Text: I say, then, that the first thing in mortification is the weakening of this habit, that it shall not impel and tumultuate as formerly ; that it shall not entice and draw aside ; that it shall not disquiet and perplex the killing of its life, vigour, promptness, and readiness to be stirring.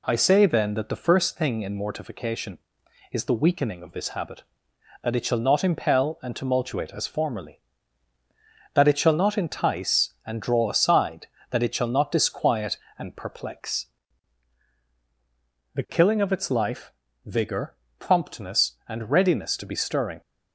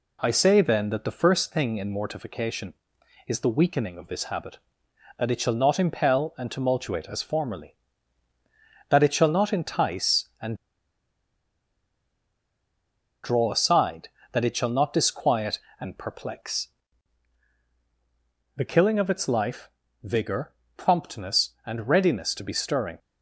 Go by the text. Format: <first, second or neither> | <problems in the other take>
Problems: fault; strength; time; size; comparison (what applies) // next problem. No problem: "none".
first | pauses between "and" and "draw"; strong; at 10.5 s; 2.6 s long // pauses between "perplex" and "the"; strong; at 16.6 s; 1.8 s long; strong in the first